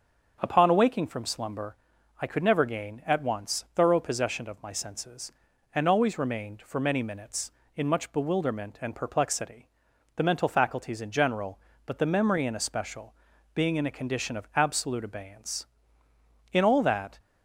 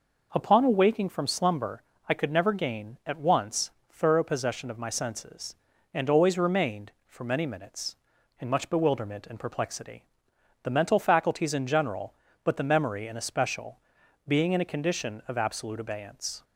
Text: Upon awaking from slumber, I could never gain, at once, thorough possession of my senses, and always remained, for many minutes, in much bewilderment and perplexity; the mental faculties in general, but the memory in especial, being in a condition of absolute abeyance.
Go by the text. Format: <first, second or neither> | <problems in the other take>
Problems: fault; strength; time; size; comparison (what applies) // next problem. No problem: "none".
second | starts louder than the rest; until 1.4 s; 7 dB // goes on to say "In all that"; noticeable; from 16.5 s on; 0.66 s long